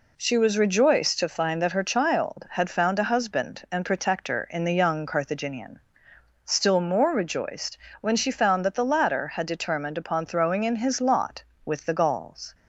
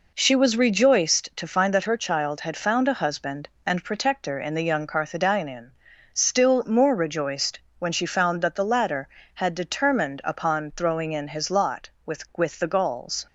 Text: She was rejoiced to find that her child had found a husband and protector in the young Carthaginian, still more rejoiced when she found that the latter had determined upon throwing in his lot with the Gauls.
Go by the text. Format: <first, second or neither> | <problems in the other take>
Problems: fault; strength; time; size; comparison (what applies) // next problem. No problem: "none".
first | pauses between "rejoiced" and "when"; slight; at 7.5 s; 0.20 s long; slight in the first // says "with" twice; at 12.3 s